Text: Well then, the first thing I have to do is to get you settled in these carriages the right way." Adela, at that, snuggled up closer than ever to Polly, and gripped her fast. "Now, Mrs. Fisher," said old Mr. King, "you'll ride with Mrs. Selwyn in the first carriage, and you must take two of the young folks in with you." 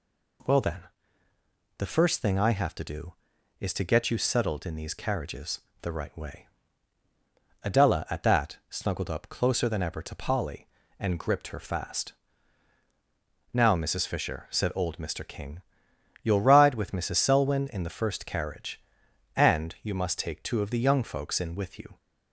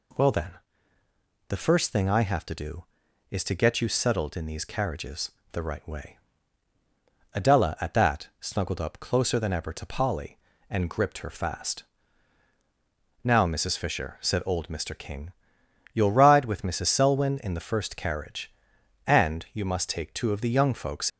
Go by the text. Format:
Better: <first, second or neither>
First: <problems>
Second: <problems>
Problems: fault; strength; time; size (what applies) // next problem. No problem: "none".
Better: first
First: pauses between "carriages" and "the"; slight; at 5.6 s; 0.22 s long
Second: pauses between "carriages" and "the"; slight; at 5.3 s; 0.22 s long // stops before "in with you"; at 21.0 s